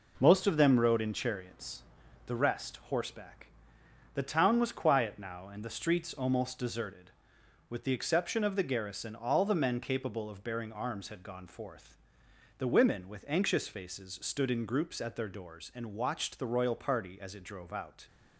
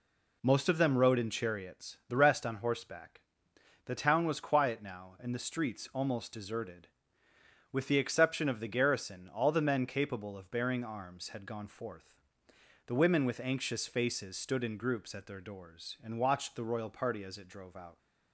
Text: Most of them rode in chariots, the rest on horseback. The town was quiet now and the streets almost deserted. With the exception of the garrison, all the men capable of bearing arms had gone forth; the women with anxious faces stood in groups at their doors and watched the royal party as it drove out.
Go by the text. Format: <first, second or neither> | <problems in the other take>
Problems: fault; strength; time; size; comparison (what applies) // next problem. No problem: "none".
second | skips "on"; at 2.8 s